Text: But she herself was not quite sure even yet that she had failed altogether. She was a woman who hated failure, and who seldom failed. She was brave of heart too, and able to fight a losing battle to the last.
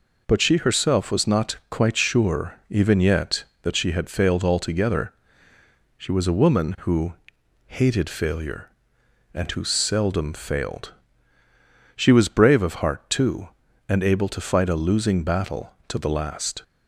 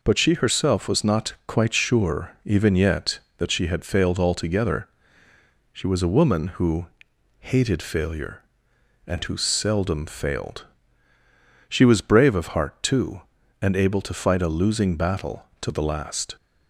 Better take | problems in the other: neither | pauses between "who" and "hated"; noticeable; the same in both

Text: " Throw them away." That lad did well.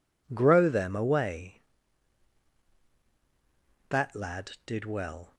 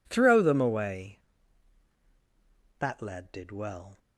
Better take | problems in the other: second | says "Grow" for "Throw"; at 0.3 s

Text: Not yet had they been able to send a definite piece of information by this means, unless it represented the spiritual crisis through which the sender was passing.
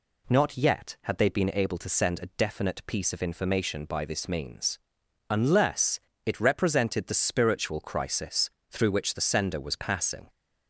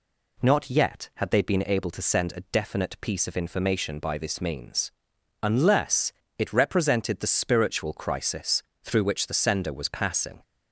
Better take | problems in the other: neither | pauses between "unless" and "it"; slight; the same in both // pauses between "crisis" and "through"; slight; the same in both

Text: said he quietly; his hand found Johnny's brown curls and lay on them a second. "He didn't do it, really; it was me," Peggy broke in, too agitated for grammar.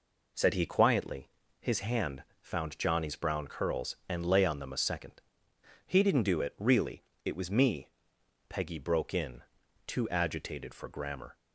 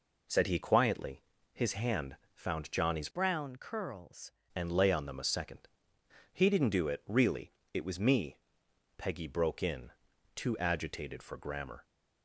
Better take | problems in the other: first | pauses between "hand" and "found"; slight; at 2.1 s; 0.18 s long; slight in the first // changes voice from "brown" to "curls"; from 3.1 to 4.3 s; 1.2 s long

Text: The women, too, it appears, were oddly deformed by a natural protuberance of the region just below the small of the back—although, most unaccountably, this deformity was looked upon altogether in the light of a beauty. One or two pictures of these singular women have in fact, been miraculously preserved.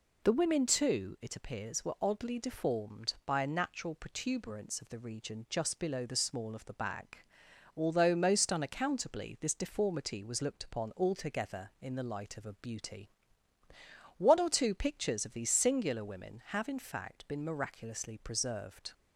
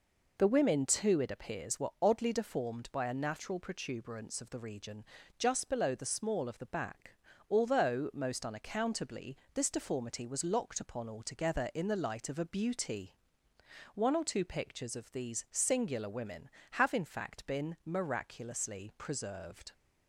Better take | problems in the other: first | pauses between "region" and "just"; slight; at 5.0 s; 0.36 s long // says "locked" for "looked"; at 10.4 s

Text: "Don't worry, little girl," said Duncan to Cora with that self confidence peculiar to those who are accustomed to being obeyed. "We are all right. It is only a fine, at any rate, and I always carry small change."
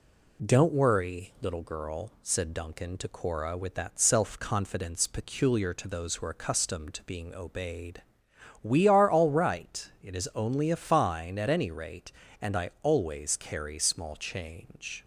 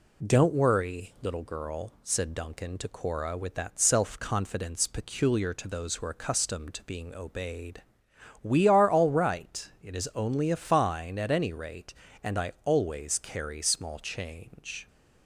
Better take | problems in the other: neither | none

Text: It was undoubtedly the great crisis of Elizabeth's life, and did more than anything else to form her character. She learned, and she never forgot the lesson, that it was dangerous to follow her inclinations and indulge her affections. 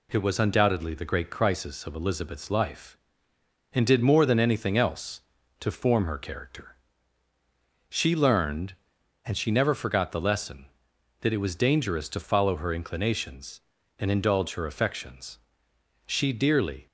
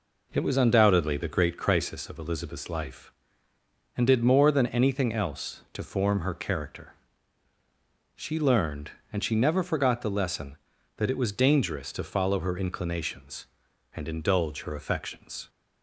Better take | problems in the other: second | goes on to say "She dearly"; noticeable; from 16.0 s on; 0.80 s long

